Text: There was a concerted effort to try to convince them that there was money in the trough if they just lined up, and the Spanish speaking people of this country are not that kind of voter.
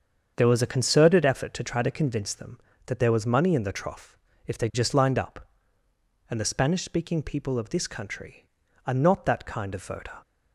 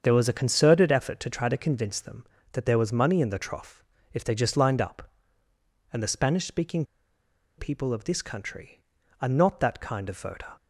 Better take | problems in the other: first | starts louder than the rest; strong; until 1.0 s; 7 dB; strong in the first // pauses between "trough" and "if"; slight; at 3.8 s; 0.30 s long; slight in the first // pauses between "speaking" and "people"; noticeable; at 6.8 s; 0.73 s long

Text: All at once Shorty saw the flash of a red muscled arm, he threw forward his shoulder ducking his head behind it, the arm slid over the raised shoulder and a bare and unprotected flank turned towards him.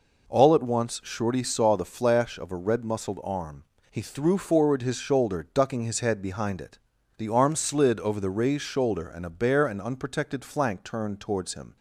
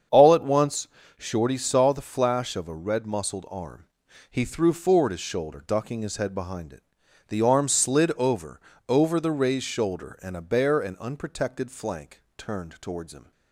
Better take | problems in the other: first | starts louder than the rest; strong; until 1.4 s; 7.5 dB // pauses between "once" and "Shorty"; slight; at 0.8 s; 0.30 s long // says "over" twice; at 8.8 s

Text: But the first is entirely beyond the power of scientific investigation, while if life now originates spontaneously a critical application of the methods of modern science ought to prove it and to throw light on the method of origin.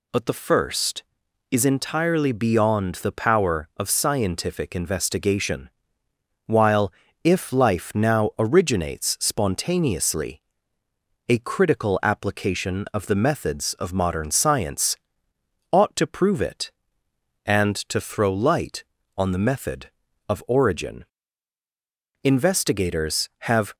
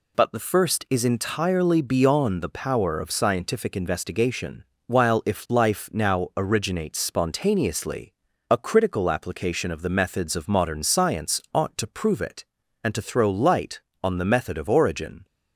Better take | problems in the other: second | pauses between "while" and "if"; slight; at 6.9 s; 0.32 s long // pauses between "spontaneously" and "a"; noticeable; at 10.4 s; 0.86 s long; also in the second // pauses between "science" and "ought"; noticeable; at 14.9 s; 0.73 s long // goes on to say "Investigators have"; from 22.2 s on; 1.5 s long

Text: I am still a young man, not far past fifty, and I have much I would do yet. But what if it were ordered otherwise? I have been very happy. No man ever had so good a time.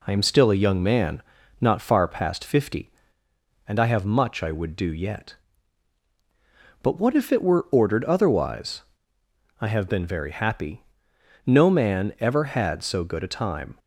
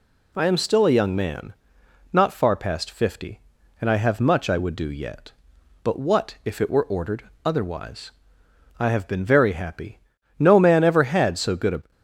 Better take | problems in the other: first | pauses between "ordered" and "otherwise"; slight; at 7.2 s; 0.20 s long // stops before "time"; at 11.9 s

